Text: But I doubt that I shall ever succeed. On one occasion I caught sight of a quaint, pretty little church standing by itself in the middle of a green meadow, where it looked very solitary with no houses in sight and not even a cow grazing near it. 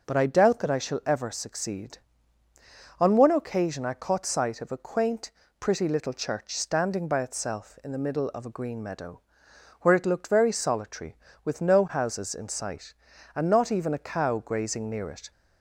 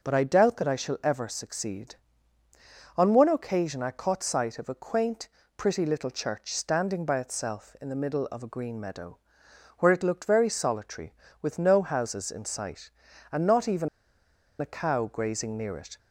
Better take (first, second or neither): first